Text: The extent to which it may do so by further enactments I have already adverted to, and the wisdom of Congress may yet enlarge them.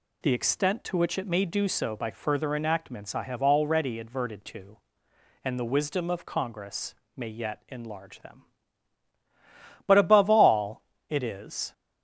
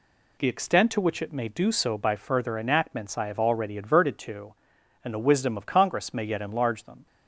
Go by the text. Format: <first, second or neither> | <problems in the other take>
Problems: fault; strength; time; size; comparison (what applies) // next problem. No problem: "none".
second | pauses between "Congress" and "may"; slight; at 6.9 s; 0.22 s long // goes on to say "But above all it is"; strong; from 9.8 s on; 1.8 s long